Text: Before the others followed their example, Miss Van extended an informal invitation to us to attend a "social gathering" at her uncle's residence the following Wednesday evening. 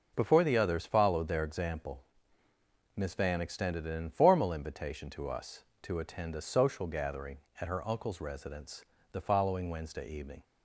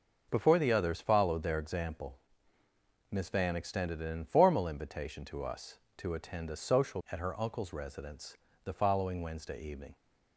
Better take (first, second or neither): first